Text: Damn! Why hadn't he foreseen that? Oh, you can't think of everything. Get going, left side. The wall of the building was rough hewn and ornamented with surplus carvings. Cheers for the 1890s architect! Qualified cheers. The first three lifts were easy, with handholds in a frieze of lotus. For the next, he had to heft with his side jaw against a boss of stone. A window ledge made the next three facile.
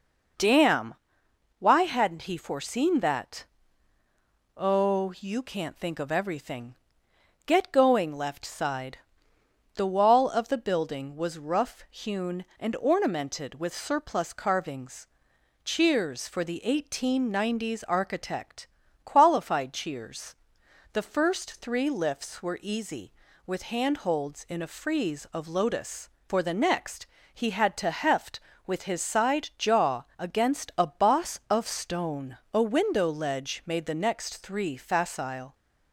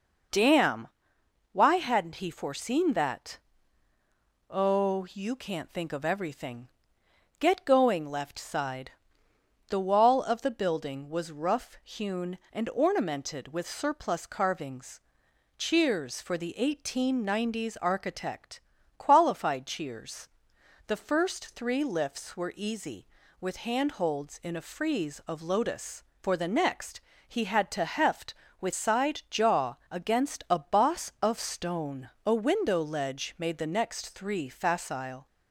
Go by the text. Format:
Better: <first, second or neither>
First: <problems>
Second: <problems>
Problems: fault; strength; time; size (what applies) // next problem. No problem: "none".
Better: first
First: none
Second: skips "his"; at 28.7 s